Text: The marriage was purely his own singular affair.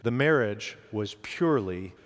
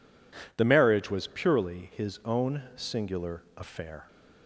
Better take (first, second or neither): second